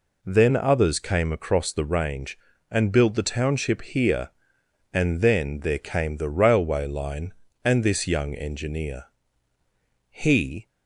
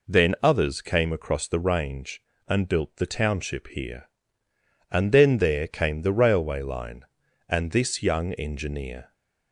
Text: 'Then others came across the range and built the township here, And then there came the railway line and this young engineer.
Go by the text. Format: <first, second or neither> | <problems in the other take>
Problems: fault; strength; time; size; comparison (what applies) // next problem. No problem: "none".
second | goes on to say "He"; from 10.1 s on; 0.56 s long